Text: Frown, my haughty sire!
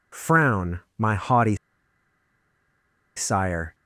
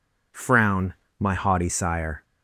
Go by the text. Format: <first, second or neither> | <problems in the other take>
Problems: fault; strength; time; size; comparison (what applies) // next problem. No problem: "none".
second | pauses between "haughty" and "sire"; strong; at 1.5 s; 1.6 s long